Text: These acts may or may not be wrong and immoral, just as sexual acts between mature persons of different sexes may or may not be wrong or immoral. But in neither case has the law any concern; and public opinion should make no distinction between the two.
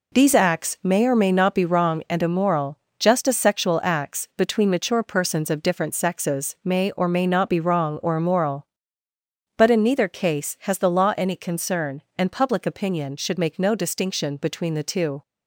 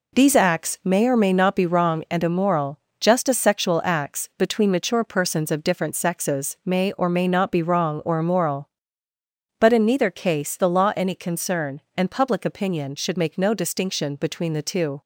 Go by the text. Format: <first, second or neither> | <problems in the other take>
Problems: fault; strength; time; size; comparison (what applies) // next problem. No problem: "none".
first | skips "has"; at 10.5 s